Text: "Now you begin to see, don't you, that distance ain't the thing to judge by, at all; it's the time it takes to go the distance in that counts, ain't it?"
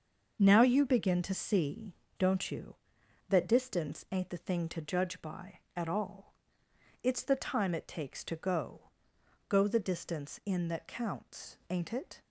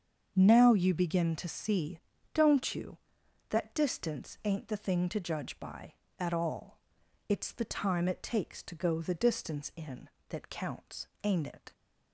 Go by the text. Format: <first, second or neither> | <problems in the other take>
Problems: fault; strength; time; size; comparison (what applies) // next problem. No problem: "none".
second | starts louder than the rest; until 1.4 s; 6.5 dB; also in the second // says "go" twice; at 9.4 s